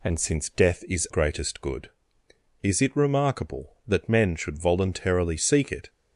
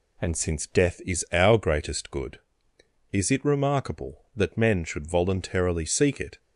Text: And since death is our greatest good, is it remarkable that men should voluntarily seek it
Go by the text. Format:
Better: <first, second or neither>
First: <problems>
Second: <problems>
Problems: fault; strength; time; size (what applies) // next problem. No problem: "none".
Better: second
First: skips "our"; at 1.0 s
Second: none